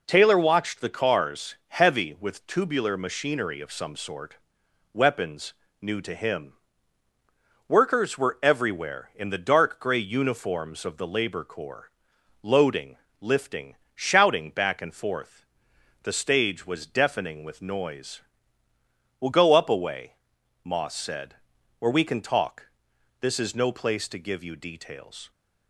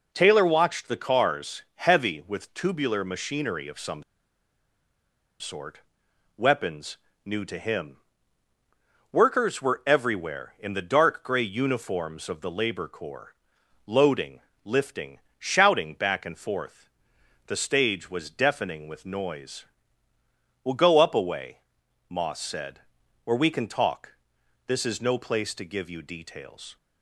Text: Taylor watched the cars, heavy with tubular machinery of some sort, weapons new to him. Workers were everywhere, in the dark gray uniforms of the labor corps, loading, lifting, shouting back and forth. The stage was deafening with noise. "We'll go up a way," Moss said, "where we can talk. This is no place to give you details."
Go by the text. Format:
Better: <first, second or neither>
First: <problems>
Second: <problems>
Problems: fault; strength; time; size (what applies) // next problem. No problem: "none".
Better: first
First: pauses between "weapons" and "new"; slight; at 5.5 s; 0.28 s long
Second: pauses between "some" and "sort"; strong; at 4.0 s; 1.3 s long // pauses between "weapons" and "new"; slight; at 6.9 s; 0.28 s long